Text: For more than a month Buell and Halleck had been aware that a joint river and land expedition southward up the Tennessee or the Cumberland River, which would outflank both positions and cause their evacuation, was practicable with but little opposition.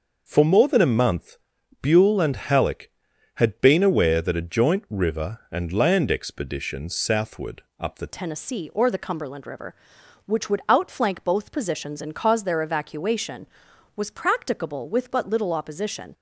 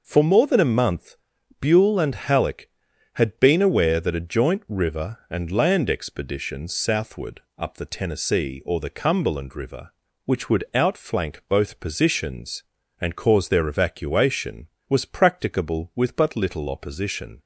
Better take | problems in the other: second | starts louder than the rest; noticeable; until 1.2 s; 6 dB // pauses between "month" and "Buell"; at 1.3 s; 0.44 s long; also in the second // pauses between "southward" and "up"; slight; at 7.6 s; 0.18 s long; slight in the second // changes voice at "Tennessee"; from 8.0 s on; 8.1 s long

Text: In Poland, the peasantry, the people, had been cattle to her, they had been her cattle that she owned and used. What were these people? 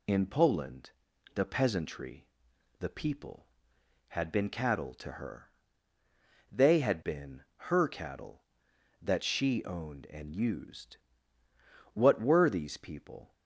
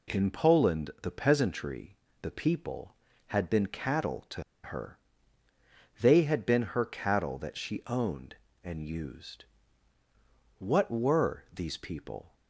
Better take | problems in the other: first | pauses between "to" and "her"; slight; at 4.4 s; 0.22 s long

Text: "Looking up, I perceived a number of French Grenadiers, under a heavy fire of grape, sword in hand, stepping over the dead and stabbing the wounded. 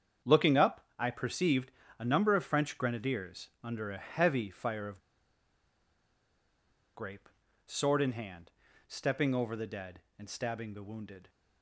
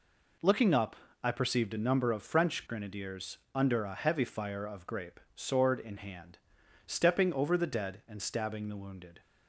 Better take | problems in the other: second | starts louder than the rest; strong; until 1.3 s; 7.5 dB // pauses between "perceived" and "a"; slight; at 1.7 s; 0.26 s long // pauses between "of" and "grape"; strong; at 5.0 s; 1.9 s long

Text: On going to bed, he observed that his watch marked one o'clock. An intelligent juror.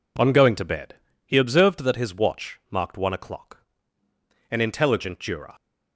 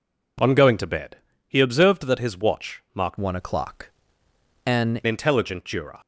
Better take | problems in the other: first | changes voice from "one" to "An"; from 3.1 to 4.9 s; 1.8 s long

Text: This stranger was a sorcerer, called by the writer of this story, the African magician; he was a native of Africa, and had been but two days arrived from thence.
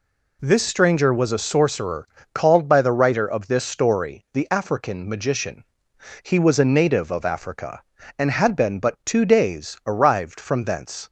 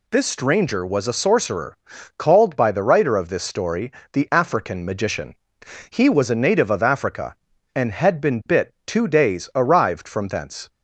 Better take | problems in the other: first | says "bit" for "but"; at 8.4 s

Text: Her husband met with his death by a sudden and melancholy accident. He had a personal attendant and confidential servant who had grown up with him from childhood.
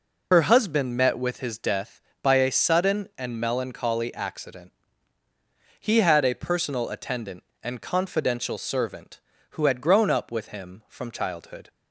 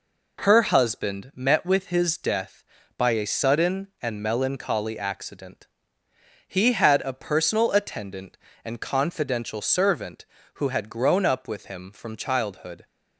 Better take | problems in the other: second | loses the start of "Her"; at 0.3 s; 60 ms

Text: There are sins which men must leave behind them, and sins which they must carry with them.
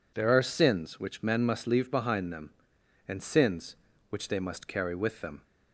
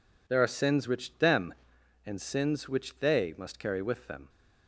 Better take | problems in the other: first | skips "men must leave behind"; at 1.1 s

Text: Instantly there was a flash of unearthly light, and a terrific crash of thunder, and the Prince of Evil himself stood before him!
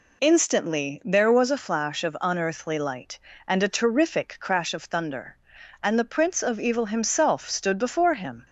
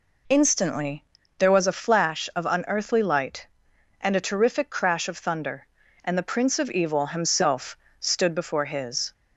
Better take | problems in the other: first | pauses between "Instantly" and "there"; slight; at 1.0 s; 0.34 s long // pauses between "himself" and "stood"; slight; at 7.7 s; 0.22 s long // says "his" for "him"; at 8.6 s

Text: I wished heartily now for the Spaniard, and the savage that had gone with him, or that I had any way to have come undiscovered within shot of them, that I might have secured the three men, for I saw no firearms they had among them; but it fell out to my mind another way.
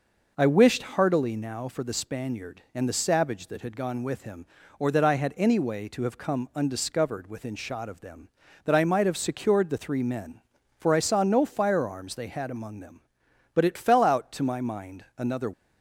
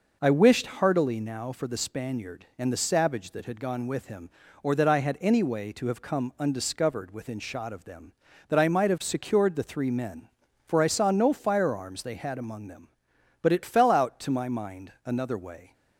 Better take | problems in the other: second | stops before "way"; at 15.5 s

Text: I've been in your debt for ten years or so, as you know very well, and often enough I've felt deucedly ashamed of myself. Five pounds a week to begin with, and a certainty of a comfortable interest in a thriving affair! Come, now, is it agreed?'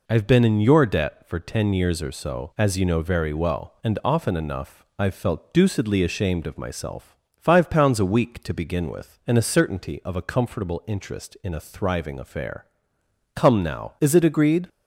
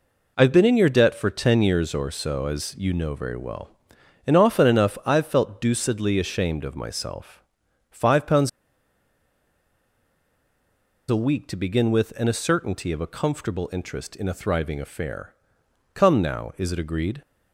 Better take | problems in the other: first | pauses between "pounds" and "a"; strong; at 8.4 s; 2.6 s long

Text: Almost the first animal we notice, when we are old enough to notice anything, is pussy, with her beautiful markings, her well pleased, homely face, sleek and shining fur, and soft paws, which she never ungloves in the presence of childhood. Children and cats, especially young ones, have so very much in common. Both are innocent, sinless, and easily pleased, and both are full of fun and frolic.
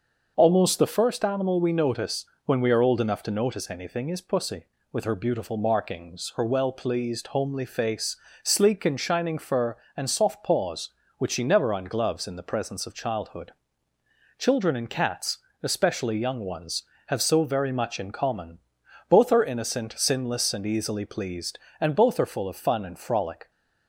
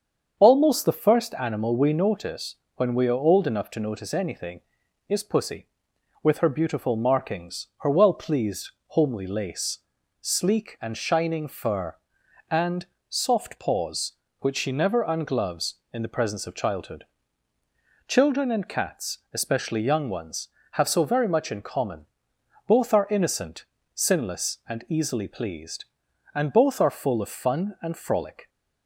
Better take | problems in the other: first | starts louder than the rest; strong; until 1.4 s; 7 dB; noticeable in the first // says "lace" for "face"; at 9.2 s // pauses between "and" and "soft"; slight; at 12.8 s; 0.22 s long

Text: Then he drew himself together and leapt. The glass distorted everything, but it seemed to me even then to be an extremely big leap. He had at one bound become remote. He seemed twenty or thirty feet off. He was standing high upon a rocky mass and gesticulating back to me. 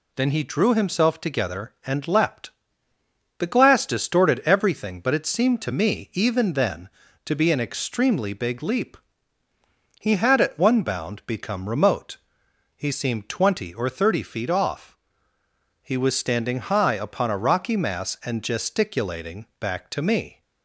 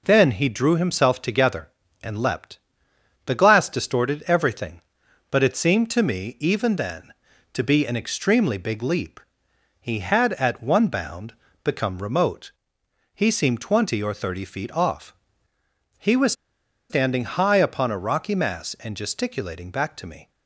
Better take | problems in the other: first | pauses between "bound" and "become"; slight; at 11.3 s; 0.30 s long // pauses between "was" and "standing"; noticeable; at 16.3 s; 0.57 s long

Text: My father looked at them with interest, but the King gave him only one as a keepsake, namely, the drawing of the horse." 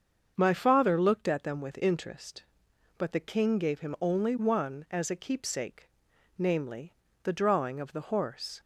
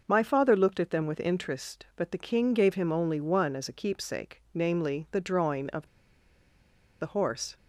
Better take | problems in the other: first | starts louder than the rest; noticeable; until 1.0 s; 6 dB; also in the first // pauses between "of" and "the"; at 5.8 s; 1.1 s long

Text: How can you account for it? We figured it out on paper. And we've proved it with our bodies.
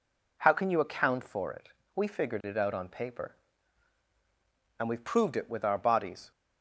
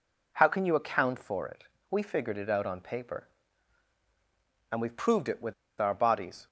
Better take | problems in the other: first | pauses between "with" and "our"; slight; at 5.5 s; 0.26 s long

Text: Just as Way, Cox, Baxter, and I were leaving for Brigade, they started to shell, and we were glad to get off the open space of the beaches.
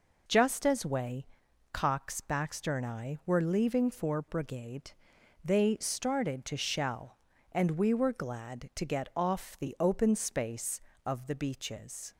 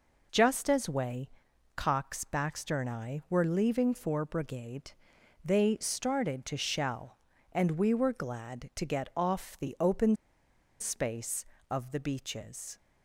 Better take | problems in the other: first | pauses between "open" and "space"; noticeable; at 10.1 s; 0.64 s long

